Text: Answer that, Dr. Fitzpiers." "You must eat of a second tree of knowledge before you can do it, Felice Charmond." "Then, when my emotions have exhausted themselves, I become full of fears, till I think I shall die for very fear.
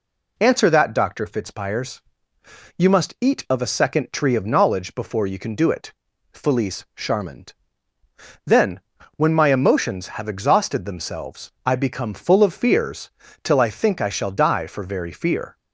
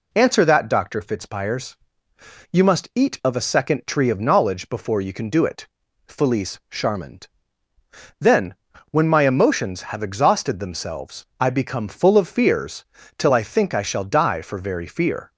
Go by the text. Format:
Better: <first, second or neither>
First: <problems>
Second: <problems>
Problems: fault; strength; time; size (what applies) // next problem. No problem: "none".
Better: neither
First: none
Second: none